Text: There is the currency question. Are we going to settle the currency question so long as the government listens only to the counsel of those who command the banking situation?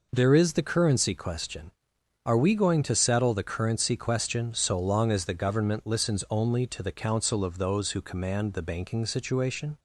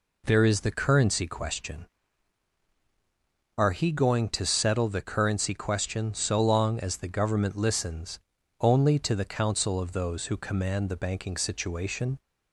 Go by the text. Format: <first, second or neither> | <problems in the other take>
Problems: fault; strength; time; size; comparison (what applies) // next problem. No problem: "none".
first | says "he" for "we"; at 3.7 s // pauses between "listens" and "only"; at 8.1 s; 0.40 s long